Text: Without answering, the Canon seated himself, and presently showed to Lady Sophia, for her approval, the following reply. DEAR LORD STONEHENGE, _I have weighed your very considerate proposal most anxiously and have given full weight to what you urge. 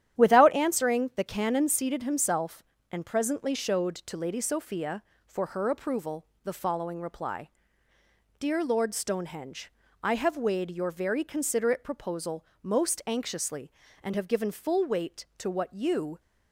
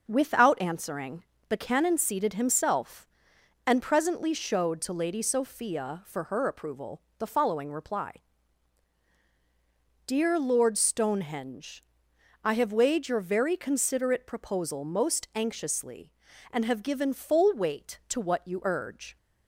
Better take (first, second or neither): second